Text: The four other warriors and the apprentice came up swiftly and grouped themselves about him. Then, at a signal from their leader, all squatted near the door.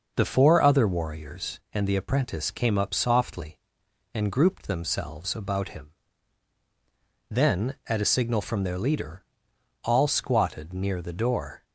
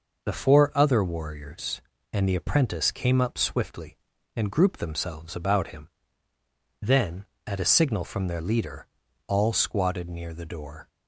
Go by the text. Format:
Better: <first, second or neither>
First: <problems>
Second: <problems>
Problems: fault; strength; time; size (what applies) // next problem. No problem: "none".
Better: second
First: says "softly" for "swiftly"; at 2.9 s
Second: none